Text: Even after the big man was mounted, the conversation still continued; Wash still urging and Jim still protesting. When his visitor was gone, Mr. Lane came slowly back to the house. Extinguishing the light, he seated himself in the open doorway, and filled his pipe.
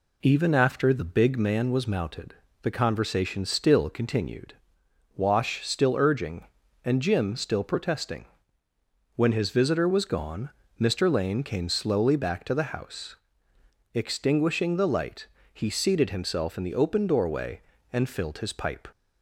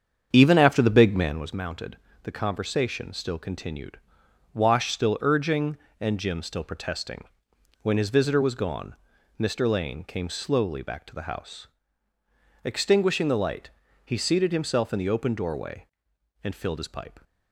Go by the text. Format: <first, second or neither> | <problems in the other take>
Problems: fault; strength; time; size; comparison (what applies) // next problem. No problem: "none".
first | starts louder than the rest; strong; until 1.5 s; 7.5 dB